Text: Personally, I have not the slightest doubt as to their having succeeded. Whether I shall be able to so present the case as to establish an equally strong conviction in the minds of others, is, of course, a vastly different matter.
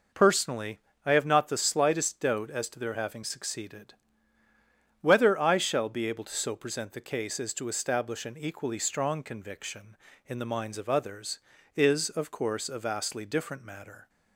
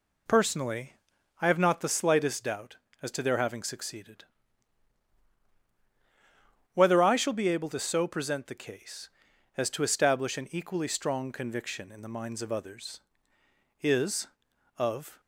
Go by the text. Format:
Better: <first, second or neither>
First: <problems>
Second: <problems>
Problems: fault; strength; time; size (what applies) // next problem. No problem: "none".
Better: first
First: none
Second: stops before "course a vastly different matter"; at 15.1 s